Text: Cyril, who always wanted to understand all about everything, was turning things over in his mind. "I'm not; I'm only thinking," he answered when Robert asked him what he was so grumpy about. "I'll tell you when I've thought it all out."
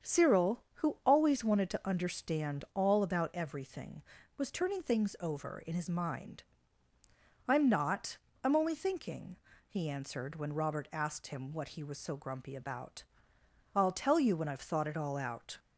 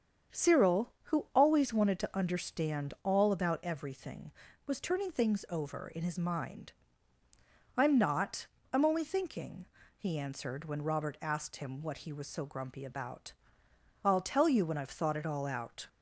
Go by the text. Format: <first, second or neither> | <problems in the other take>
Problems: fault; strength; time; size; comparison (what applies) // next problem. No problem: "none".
neither | starts louder than the rest; strong; the same in both